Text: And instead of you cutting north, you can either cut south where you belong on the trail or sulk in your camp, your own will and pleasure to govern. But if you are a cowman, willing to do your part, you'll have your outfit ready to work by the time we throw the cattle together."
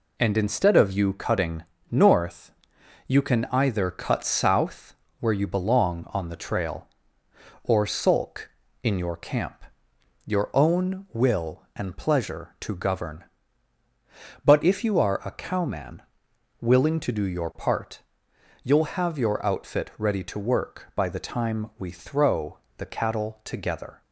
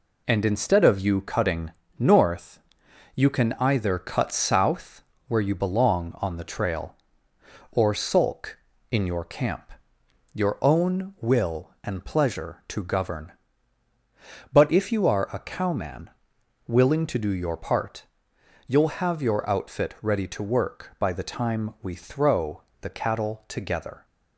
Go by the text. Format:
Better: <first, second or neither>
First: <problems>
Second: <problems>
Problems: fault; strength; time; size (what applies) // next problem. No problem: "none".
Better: neither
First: pauses between "cutting" and "north"; slight; at 1.6 s; 0.26 s long // pauses between "south" and "where"; slight; at 4.9 s; 0.26 s long // pauses between "throw" and "the"; slight; at 22.5 s; 0.22 s long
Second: pauses between "cutting" and "north"; slight; at 1.7 s; 0.26 s long // pauses between "south" and "where"; slight; at 5.0 s; 0.26 s long // pauses between "throw" and "the"; slight; at 22.6 s; 0.22 s long